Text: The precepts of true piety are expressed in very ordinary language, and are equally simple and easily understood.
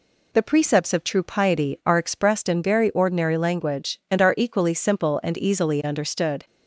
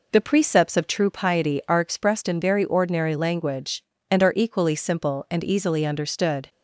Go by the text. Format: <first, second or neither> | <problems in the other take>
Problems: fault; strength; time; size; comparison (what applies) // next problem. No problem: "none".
first | starts louder than the rest; noticeable; until 1.3 s; 4 dB